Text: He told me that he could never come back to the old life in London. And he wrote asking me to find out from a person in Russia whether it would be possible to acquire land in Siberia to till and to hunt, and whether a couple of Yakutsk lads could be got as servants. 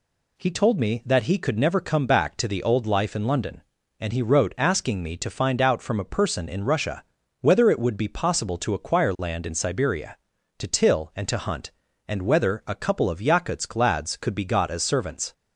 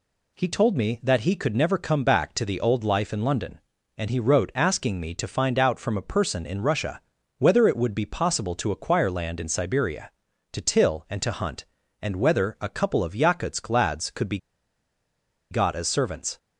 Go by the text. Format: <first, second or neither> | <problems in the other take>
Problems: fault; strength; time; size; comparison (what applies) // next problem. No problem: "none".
first | pauses between "Russia" and "whether"; at 7.0 s; 0.38 s long; also in the first // pauses between "be" and "got"; at 14.3 s; 1.1 s long